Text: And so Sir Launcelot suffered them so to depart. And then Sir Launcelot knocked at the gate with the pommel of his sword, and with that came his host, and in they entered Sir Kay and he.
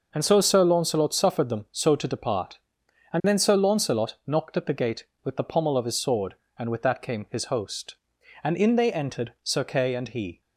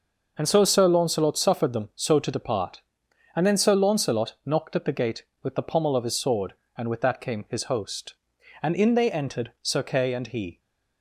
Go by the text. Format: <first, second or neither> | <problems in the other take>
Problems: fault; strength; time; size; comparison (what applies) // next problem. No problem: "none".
neither | none